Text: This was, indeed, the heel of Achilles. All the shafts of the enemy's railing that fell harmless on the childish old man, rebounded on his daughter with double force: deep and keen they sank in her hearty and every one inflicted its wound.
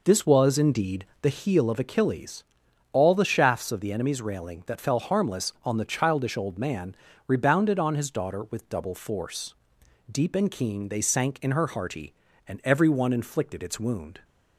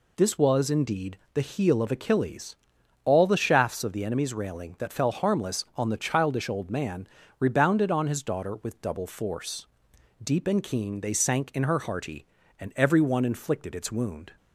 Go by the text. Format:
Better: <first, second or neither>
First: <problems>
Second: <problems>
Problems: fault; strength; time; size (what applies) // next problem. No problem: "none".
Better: second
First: starts louder than the rest; noticeable; until 1.5 s; 4.5 dB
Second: none